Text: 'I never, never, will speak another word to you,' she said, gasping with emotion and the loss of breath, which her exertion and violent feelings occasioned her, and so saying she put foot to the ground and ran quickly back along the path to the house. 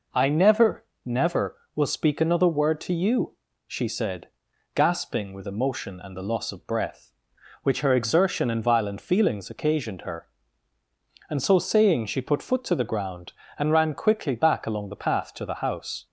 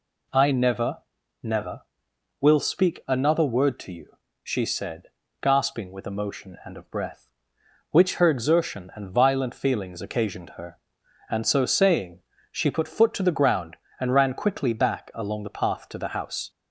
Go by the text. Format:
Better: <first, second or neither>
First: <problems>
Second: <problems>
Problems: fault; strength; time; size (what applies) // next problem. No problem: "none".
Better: first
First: none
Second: skips "the loss"; at 6.7 s // pauses between "saying" and "she"; slight; at 12.2 s; 0.32 s long